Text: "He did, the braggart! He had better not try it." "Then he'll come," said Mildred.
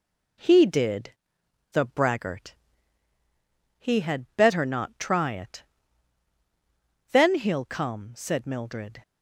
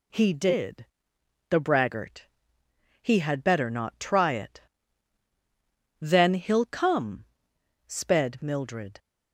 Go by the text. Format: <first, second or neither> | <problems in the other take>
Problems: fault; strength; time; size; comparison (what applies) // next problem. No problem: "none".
first | says "sped" for "said"; at 7.8 s